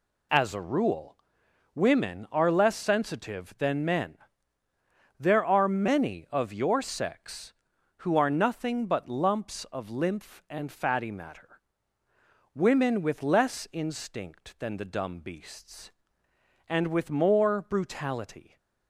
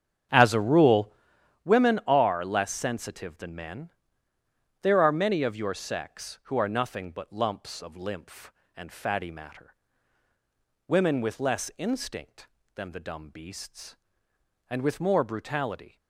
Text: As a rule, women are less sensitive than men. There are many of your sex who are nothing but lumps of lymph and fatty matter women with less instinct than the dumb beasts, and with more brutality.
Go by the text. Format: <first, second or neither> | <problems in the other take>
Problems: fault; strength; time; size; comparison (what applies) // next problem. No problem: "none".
first | starts louder than the rest; strong; until 1.6 s; 8.5 dB // pauses between "matter" and "women"; at 9.7 s; 1.1 s long; also in the first